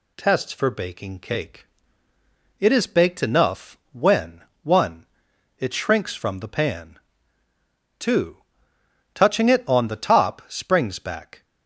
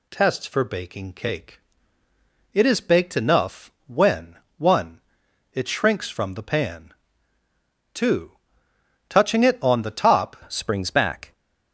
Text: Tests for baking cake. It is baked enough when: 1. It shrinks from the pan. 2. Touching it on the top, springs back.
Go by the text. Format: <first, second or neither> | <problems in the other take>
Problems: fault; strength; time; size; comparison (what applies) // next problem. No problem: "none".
first | pauses between "enough" and "when"; slight; at 3.7 s; 0.16 s long; slight in the first // changes voice at "springs"; from 10.5 s on; 0.8 s long